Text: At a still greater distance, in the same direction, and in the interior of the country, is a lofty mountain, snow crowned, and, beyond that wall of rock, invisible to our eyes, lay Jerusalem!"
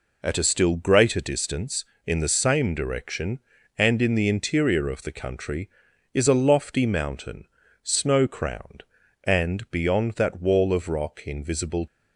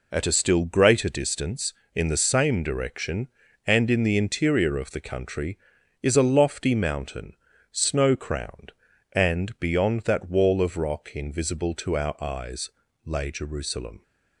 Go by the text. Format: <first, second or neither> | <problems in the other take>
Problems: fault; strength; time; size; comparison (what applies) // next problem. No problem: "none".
second | stops before "to our eyes lay Jerusalem"; at 11.8 s